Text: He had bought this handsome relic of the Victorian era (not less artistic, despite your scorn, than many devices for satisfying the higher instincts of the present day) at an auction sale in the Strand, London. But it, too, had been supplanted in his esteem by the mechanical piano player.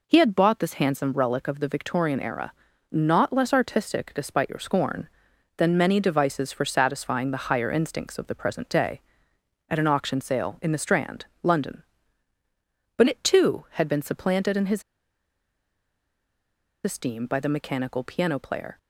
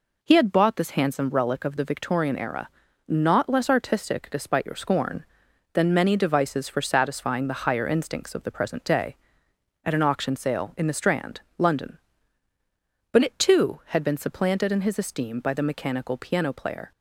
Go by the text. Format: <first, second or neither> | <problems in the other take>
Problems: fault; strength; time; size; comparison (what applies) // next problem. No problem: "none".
second | pauses between "his" and "esteem"; strong; at 14.8 s; 2.0 s long